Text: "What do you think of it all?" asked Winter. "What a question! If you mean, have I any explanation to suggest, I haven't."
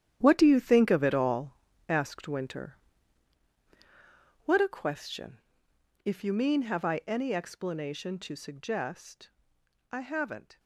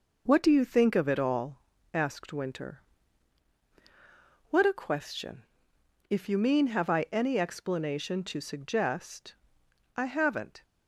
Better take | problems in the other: second | gets quieter; strong; throughout; 12 dB

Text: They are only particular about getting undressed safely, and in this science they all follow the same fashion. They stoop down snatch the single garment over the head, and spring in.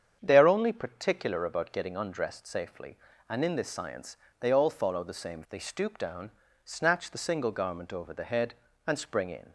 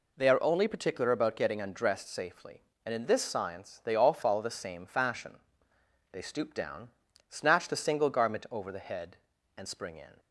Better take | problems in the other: second | starts louder than the rest; strong; until 1.2 s; 7.5 dB // pauses between "science" and "they"; slight; at 4.1 s; 0.24 s long // skips "fashion"; at 5.4 s // pauses between "down" and "snatch"; slight; at 6.3 s; 0.34 s long; also in the second

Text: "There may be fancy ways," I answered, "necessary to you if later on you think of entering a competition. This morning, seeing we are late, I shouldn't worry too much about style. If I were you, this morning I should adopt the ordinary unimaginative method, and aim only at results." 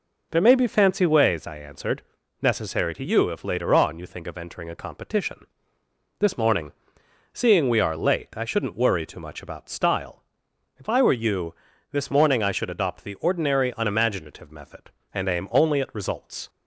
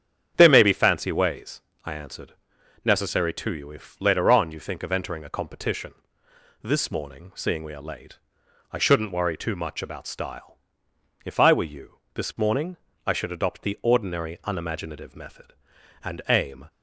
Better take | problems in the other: first | starts louder than the rest; strong; until 1.3 s; 8.5 dB // pauses between "morning" and "I"; slight; at 12.7 s; 0.28 s long // stops before "only at results"; at 16.6 s

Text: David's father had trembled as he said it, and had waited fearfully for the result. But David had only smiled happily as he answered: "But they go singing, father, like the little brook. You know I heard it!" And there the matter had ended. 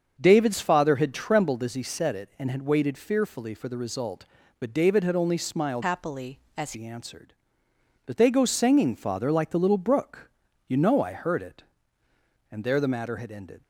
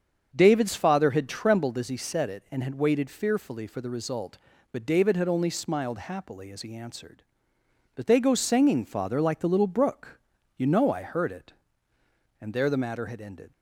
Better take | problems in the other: second | starts louder than the rest; until 1.2 s; 6.5 dB; also in the second // changes voice from "happily" to "as"; from 5.8 to 6.7 s; 0.9 s long

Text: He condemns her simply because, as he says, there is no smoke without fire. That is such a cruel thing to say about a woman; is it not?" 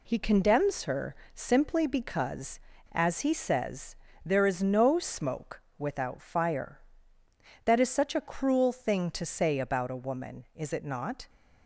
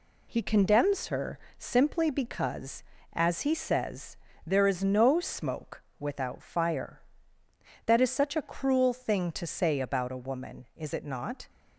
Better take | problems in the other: neither | pauses between "her" and "simply"; slight; the same in both // pauses between "smoke" and "without"; slight; the same in both

